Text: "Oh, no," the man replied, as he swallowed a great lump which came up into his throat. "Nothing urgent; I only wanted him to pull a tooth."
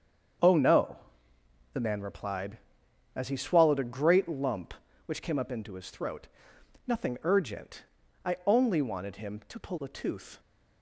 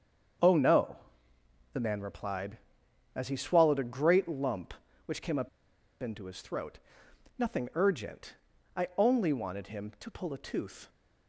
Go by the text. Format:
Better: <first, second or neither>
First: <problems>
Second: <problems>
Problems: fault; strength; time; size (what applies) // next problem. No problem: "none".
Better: first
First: starts louder than the rest; strong; until 2.2 s; 7 dB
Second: starts louder than the rest; strong; until 2.2 s; 7 dB // pauses between "up" and "into"; noticeable; at 5.4 s; 0.53 s long